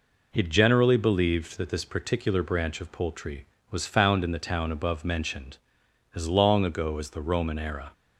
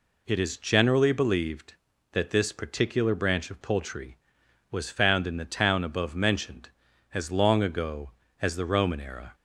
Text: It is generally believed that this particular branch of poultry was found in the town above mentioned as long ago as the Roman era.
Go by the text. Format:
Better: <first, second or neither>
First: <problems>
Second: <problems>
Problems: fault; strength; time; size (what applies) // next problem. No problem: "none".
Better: second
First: skips "is"; at 0.4 s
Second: none